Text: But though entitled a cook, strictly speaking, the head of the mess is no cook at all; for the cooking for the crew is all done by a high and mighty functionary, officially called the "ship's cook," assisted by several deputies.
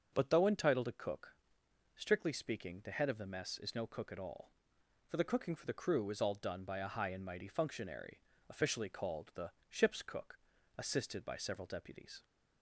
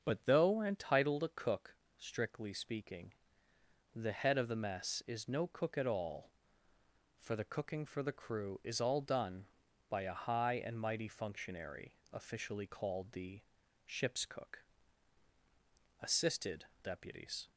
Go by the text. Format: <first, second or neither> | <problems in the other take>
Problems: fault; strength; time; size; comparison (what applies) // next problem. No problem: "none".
first | starts louder than the rest; until 1.0 s; 6.5 dB; noticeable in the first // pauses between "the" and "ship's"; at 13.4 s; 0.44 s long; slight in the first // skips "by several"; at 16.7 s